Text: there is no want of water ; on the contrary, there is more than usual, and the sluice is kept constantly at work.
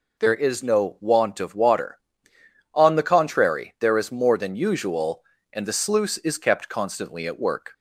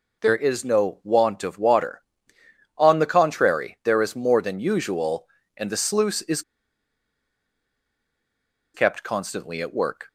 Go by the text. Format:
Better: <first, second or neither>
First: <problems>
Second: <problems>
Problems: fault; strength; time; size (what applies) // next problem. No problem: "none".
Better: first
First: none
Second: pauses between "is" and "kept"; strong; at 6.4 s; 2.3 s long